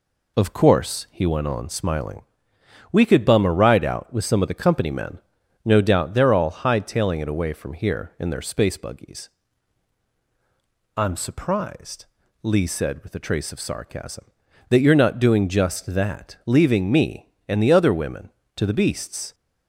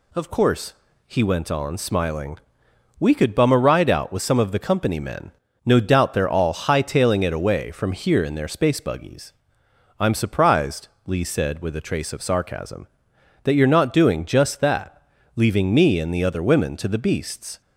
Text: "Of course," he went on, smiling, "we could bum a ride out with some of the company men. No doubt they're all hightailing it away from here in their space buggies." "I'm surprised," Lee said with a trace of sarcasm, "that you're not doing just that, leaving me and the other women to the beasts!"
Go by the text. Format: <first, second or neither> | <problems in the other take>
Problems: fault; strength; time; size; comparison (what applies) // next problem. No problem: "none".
neither | none